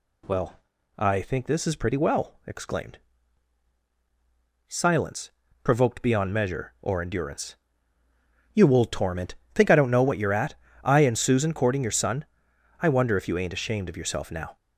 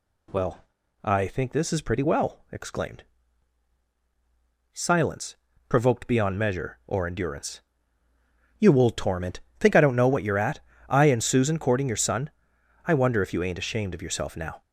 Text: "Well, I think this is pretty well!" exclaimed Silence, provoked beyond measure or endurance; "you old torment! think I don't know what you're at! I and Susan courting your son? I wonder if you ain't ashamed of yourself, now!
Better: neither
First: pauses between "exclaimed" and "Silence"; strong; at 2.9 s; 1.7 s long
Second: pauses between "exclaimed" and "Silence"; strong; at 3.0 s; 1.7 s long

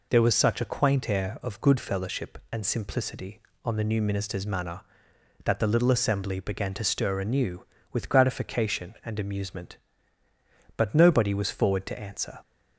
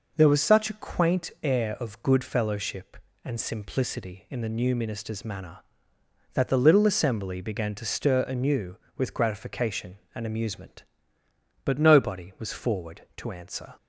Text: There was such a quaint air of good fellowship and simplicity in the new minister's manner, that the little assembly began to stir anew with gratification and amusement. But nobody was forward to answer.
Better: second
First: says "on" for "in"; at 3.6 s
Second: none

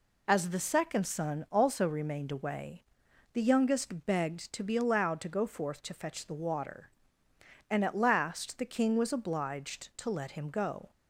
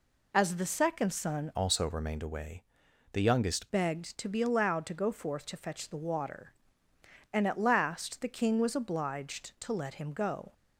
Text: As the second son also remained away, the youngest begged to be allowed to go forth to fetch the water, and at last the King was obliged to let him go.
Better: first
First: none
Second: changes voice from "also" to "youngest"; from 1.5 to 3.6 s; 2.1 s long

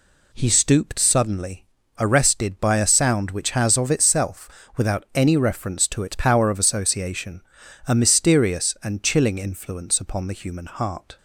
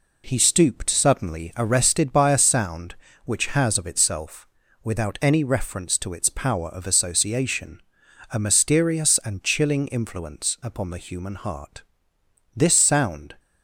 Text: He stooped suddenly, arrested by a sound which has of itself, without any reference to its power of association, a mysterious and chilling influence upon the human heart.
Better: first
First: none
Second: goes on to say "This sound"; noticeable; from 12.5 s on; 0.80 s long

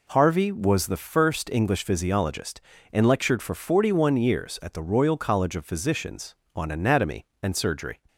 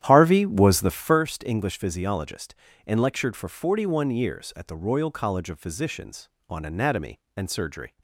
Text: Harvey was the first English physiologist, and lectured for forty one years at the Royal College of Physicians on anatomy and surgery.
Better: first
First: none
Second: starts louder than the rest; strong; until 1.2 s; 11 dB

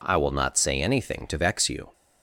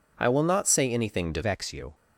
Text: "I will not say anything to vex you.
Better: first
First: none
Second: changes voice at "vex"; from 1.4 s on; 0.5 s long

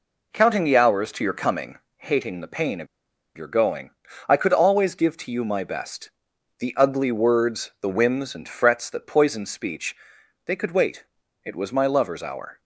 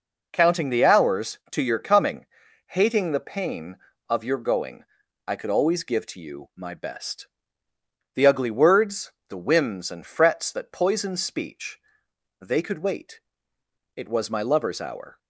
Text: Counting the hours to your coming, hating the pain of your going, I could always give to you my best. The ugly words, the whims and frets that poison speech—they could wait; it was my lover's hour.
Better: second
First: pauses between "of" and "your"; noticeable; at 2.8 s; 0.50 s long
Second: none

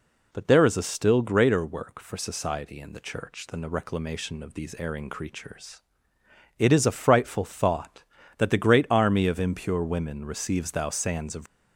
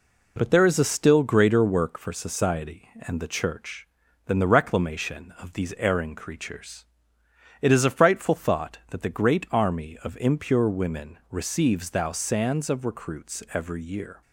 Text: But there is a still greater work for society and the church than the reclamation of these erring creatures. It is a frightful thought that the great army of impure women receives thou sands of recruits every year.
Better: second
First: stops before "recruits every year"; at 11.4 s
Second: none

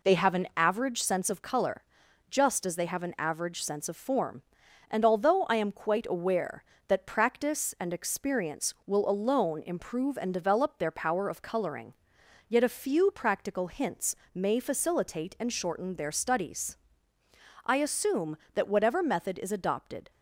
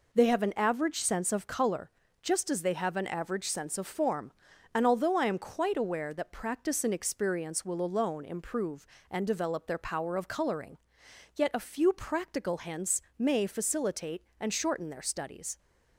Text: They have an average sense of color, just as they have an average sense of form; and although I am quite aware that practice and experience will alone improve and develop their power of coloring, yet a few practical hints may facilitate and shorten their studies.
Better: second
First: pauses between "hints" and "may"; slight; at 14.1 s; 0.18 s long // goes on to say "I assume that whatever method is adopted"; strong; from 17.6 s on; 2.4 s long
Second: pauses between "hints" and "may"; slight; at 13.0 s; 0.18 s long

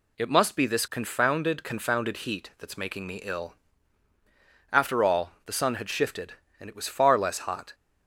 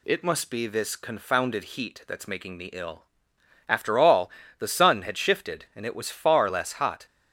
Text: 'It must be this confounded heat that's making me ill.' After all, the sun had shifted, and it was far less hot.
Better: second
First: says "confounded" twice; at 1.6 s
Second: none

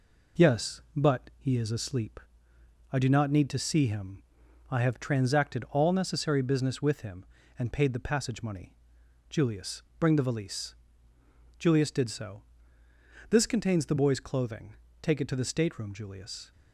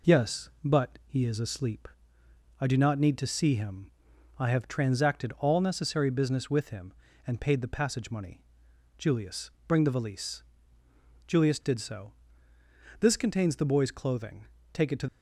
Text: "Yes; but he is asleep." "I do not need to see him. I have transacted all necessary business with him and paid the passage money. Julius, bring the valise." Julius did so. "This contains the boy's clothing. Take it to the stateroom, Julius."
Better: first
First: none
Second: stops before "the stateroom Julius"; at 15.0 s

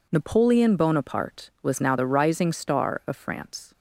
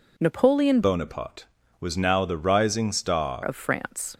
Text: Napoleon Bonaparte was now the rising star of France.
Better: first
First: none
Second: changes voice from "Bonaparte" to "star"; from 0.8 to 3.4 s; 2.6 s long

